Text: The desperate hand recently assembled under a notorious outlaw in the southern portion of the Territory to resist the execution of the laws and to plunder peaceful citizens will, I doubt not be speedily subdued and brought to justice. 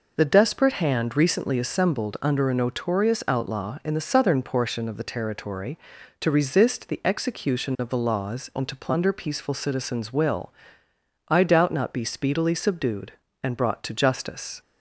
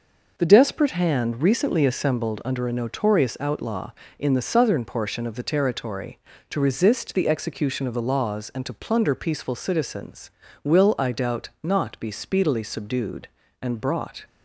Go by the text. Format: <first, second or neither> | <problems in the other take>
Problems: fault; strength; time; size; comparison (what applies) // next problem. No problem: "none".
first | stops before "to justice"; at 14.2 s